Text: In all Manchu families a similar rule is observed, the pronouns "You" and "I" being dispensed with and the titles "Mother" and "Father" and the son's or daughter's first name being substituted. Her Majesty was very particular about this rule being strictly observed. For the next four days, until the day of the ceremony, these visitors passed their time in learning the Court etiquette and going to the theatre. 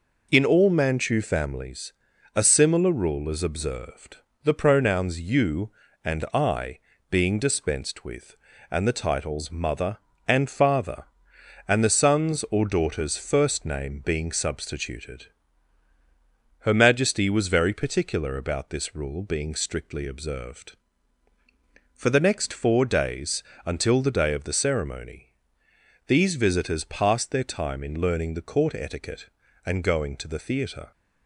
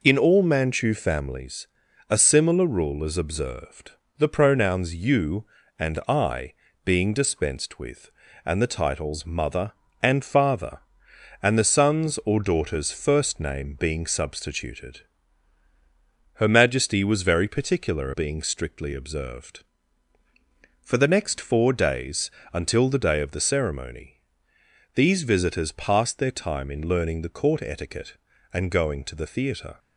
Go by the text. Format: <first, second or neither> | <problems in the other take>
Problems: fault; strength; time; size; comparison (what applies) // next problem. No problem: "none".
first | pauses between "families" and "a"; at 1.6 s; 0.42 s long; also in the first // pauses between "I" and "being"; slight; at 6.5 s; 0.30 s long; slight in the first // skips "about this rule"; at 18.1 s